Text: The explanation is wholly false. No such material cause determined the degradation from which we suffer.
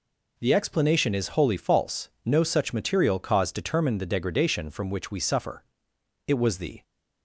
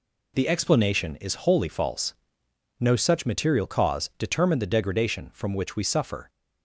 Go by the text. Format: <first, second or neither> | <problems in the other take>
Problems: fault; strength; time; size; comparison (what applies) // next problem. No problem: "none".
second | goes on to say "It was the"; from 6.2 s on; 0.56 s long